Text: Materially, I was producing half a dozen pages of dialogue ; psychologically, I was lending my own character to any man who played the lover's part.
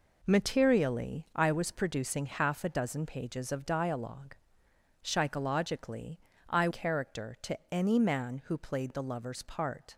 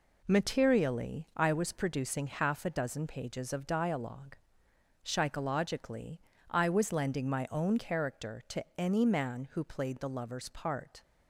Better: second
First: skips "was lending my own"; at 6.6 s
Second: none

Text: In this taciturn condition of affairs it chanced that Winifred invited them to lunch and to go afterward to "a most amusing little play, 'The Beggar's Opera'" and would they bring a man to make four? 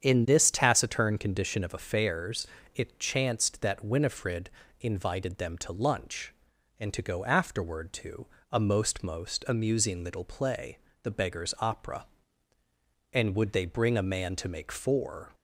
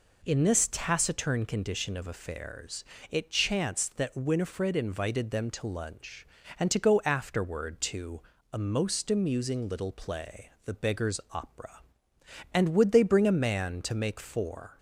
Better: second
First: starts louder than the rest; strong; until 1.0 s; 8 dB // pauses between "affairs" and "it"; slight; at 2.4 s; 0.26 s long // pauses between "Winifred" and "invited"; slight; at 4.5 s; 0.30 s long // pauses between "to" and "a"; slight; at 8.2 s; 0.24 s long // says "most" twice; at 9.0 s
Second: pauses between "affairs" and "it"; slight; at 2.8 s; 0.26 s long // pauses between "to" and "a"; slight; at 8.2 s; 0.32 s long

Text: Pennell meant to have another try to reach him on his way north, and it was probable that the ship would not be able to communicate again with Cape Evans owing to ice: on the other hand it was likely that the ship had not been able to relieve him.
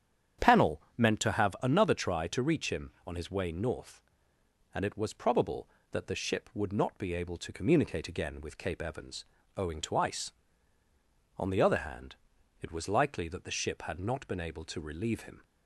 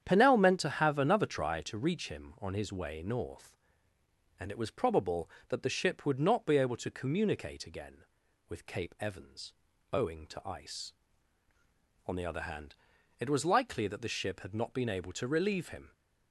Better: neither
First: starts louder than the rest; strong; until 1.5 s; 9 dB // pauses between "Evans" and "owing"; slight; at 9.2 s; 0.32 s long // pauses between "hand" and "it"; noticeable; at 12.1 s; 0.46 s long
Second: starts louder than the rest; strong; until 1.0 s; 9 dB // pauses between "Evans" and "owing"; at 9.5 s; 0.40 s long // pauses between "hand" and "it"; noticeable; at 12.7 s; 0.46 s long

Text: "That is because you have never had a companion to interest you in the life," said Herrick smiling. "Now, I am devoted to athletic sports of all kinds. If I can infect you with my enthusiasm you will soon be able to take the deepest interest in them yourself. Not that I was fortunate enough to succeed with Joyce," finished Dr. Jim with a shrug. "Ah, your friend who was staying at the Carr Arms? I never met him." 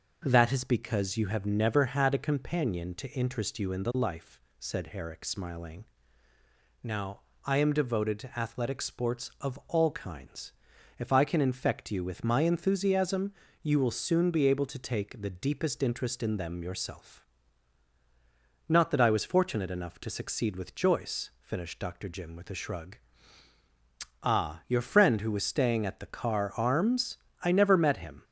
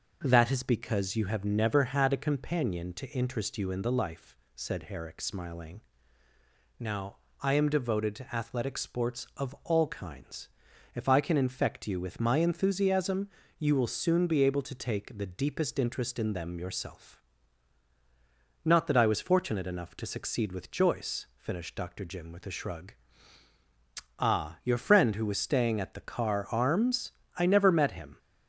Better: neither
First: pauses between "enthusiasm" and "you"; slight; at 13.3 s; 0.28 s long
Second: pauses between "enthusiasm" and "you"; slight; at 13.2 s; 0.28 s long

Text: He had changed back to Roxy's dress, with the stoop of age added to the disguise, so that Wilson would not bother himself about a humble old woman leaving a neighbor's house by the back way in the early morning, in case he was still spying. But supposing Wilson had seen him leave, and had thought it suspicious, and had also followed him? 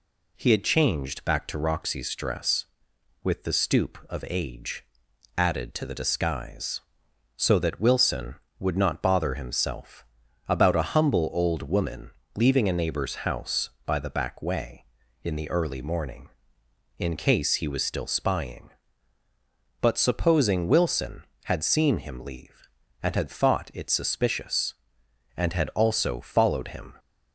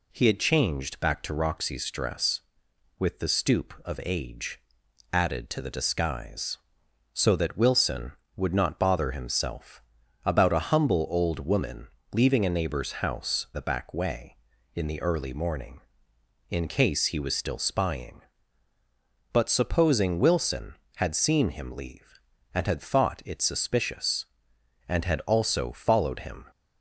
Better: first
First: pauses between "age" and "added"; noticeable; at 4.8 s; 0.52 s long // pauses between "himself" and "about"; at 10.0 s; 0.44 s long // pauses between "woman" and "leaving"; slight; at 12.0 s; 0.26 s long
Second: pauses between "age" and "added"; noticeable; at 4.6 s; 0.52 s long // pauses between "himself" and "about"; at 9.8 s; 0.44 s long // pauses between "woman" and "leaving"; slight; at 11.8 s; 0.26 s long // skips "by"; at 13.5 s

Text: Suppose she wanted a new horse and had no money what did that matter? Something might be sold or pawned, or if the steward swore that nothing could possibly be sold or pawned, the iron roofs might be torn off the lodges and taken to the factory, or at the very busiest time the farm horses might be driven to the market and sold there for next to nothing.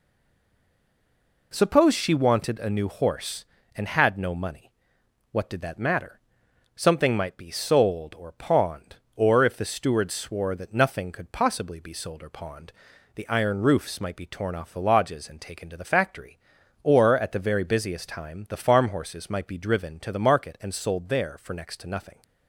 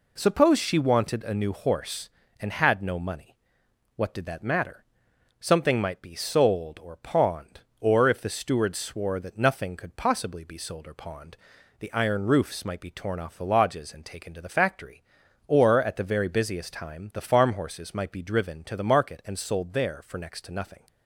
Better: second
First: stays silent before the first word; noticeable; until 1.5 s; 1.5 s long // pauses between "money" and "what"; noticeable; at 4.7 s; 0.62 s long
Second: pauses between "money" and "what"; noticeable; at 3.3 s; 0.62 s long

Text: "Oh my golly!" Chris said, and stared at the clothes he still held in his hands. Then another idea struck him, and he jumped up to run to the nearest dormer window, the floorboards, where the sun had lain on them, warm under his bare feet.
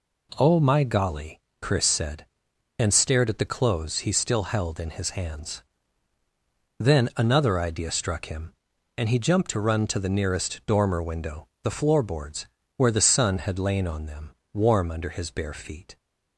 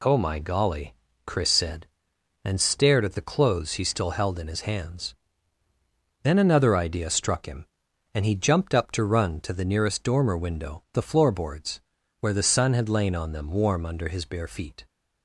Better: second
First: skips "up"; at 9.4 s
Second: none

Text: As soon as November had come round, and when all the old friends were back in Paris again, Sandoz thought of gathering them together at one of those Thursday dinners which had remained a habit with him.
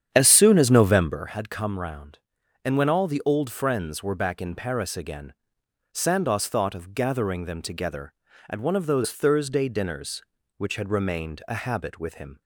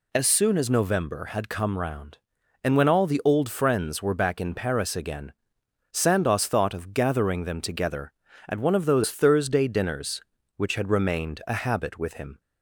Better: second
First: starts louder than the rest; strong; until 1.4 s; 9.5 dB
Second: none

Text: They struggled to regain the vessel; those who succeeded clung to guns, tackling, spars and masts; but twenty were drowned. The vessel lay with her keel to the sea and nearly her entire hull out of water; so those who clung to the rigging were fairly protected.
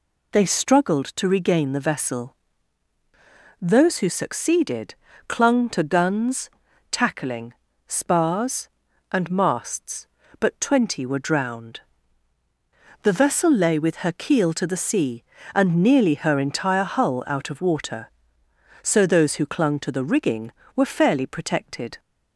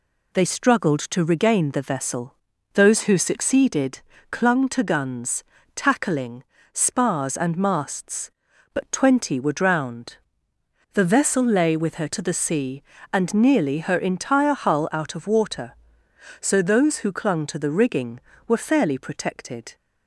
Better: first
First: pauses between "succeeded" and "clung"; slight; at 4.9 s; 0.34 s long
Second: pauses between "succeeded" and "clung"; slight; at 3.9 s; 0.30 s long // skips "keel"; at 12.0 s

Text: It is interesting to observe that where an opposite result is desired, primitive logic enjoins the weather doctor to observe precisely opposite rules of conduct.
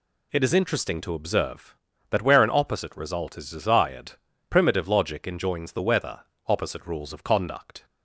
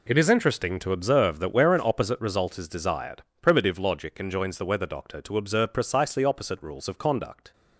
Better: second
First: skips "doctor to observe precisely"; at 6.3 s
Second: none

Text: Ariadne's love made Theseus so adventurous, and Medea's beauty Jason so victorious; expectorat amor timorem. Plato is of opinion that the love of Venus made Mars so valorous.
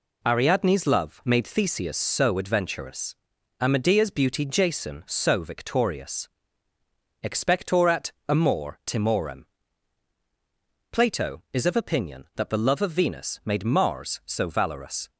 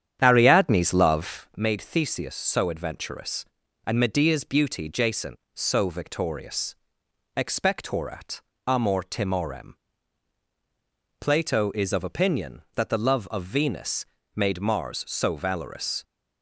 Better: first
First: pauses between "expectorat" and "amor"; slight; at 8.1 s; 0.18 s long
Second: starts louder than the rest; strong; until 1.7 s; 9 dB // pauses between "expectorat" and "amor"; slight; at 8.4 s; 0.24 s long // pauses between "Venus" and "made"; slight; at 14.0 s; 0.30 s long

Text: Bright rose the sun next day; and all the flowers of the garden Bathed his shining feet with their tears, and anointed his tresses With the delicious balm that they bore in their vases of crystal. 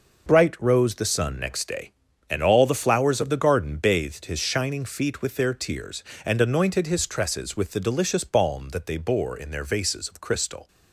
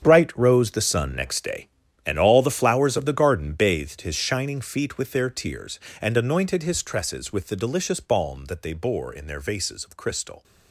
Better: first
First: none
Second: gets quieter; strong; throughout; 12.5 dB

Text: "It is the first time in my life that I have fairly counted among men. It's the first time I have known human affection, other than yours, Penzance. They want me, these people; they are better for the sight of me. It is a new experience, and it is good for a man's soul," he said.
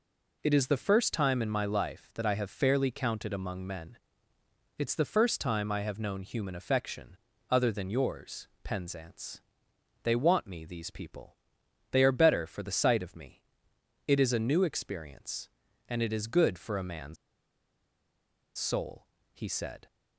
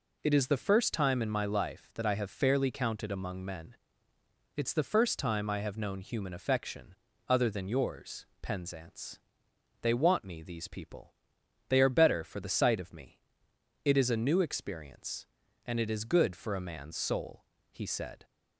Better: second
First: pauses between "man's" and "soul"; strong; at 17.1 s; 1.4 s long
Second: none

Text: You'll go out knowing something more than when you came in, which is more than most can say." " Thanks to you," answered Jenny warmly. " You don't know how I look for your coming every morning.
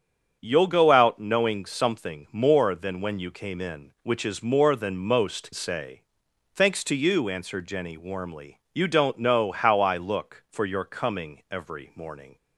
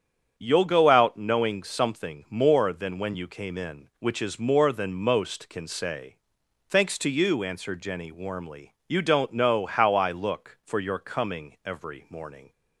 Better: second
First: starts louder than the rest; strong; until 1.4 s; 8.5 dB // skips "can"; at 5.5 s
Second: starts louder than the rest; strong; until 1.3 s; 8.5 dB

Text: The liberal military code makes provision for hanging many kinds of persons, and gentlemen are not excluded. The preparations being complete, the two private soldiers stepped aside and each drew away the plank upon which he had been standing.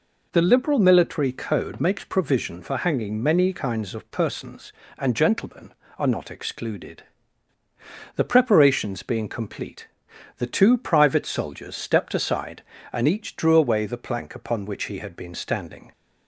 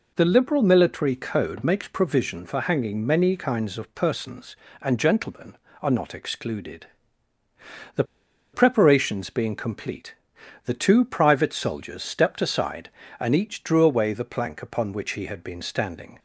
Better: first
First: none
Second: pauses between "The" and "preparations"; noticeable; at 8.0 s; 0.50 s long

